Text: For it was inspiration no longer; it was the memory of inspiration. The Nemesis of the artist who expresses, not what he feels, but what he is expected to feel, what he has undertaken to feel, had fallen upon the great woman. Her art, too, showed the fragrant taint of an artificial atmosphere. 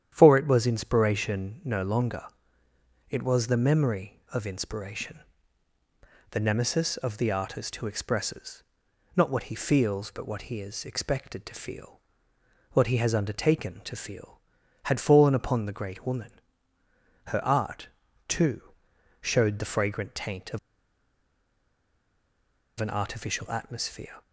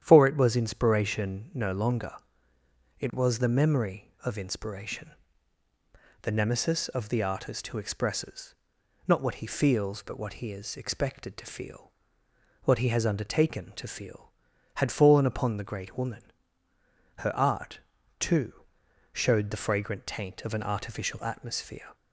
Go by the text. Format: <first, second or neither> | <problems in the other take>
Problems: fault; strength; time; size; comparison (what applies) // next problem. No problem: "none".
second | starts louder than the rest; strong; until 1.1 s; 10 dB; strong in the second // pauses between "of" and "an"; strong; at 20.5 s; 2.2 s long